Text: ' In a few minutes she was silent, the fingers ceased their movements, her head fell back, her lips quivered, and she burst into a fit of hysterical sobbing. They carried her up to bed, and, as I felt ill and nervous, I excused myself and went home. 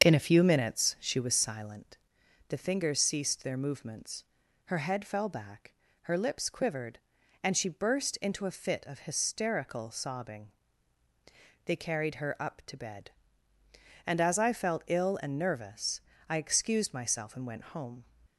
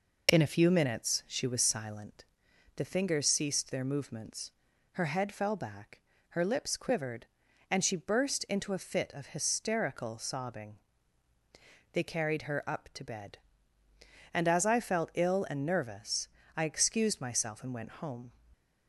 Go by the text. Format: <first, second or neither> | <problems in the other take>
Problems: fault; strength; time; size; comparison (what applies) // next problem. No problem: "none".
second | starts louder than the rest; until 1.4 s; 6.5 dB